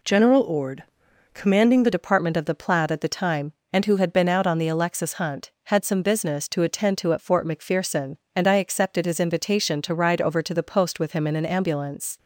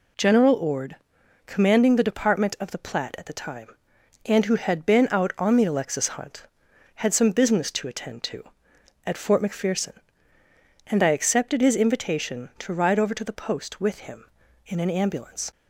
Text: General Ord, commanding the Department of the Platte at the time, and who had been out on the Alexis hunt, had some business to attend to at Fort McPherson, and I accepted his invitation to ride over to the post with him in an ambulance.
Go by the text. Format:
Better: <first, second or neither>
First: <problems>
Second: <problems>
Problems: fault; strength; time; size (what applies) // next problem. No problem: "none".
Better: second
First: changes voice at "Department"; from 1.9 s on; 10.2 s long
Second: none